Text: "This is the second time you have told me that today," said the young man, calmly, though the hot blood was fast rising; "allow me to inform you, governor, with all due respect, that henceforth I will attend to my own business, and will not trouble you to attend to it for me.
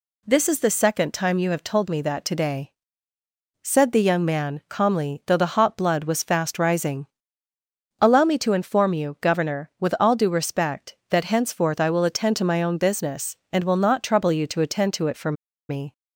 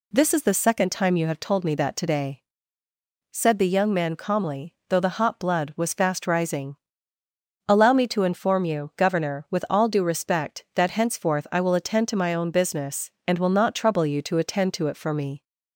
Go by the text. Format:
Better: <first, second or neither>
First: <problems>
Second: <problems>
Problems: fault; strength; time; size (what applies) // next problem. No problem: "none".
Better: second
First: pauses between "for" and "me"; at 15.3 s; 0.36 s long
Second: none